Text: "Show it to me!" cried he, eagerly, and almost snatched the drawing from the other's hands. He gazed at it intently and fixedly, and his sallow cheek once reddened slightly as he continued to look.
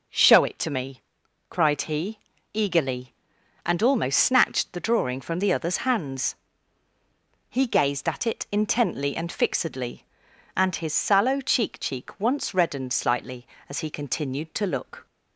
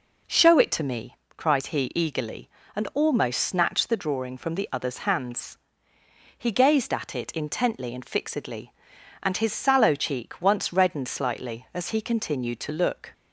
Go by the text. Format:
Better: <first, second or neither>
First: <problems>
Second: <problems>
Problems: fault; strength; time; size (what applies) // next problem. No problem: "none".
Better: second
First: says "cheek" twice; at 11.7 s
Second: none